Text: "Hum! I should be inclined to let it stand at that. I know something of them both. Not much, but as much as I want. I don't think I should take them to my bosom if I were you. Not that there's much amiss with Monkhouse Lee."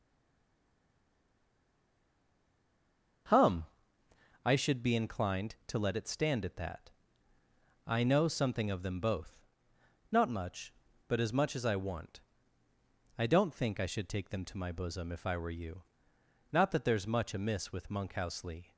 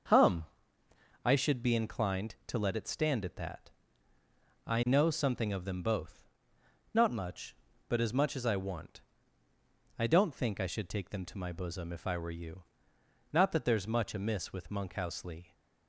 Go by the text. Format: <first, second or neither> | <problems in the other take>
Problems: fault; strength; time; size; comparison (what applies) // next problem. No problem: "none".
second | stays silent before the first word; strong; until 3.2 s; 3.2 s long // starts louder than the rest; noticeable; until 5.0 s; 6 dB; also in the second